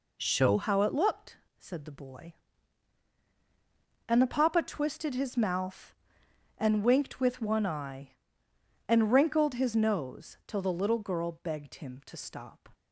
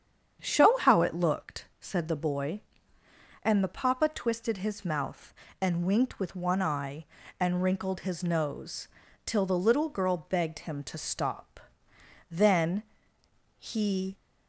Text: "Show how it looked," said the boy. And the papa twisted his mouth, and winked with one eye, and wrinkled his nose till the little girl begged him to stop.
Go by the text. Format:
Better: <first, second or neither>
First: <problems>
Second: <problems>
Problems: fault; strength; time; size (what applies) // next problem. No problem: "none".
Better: first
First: none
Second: starts louder than the rest; strong; until 1.4 s; 8 dB // pauses between "nose" and "till"; at 8.8 s; 0.38 s long // goes on to say "Then he"; strong; from 12.3 s on; 1.8 s long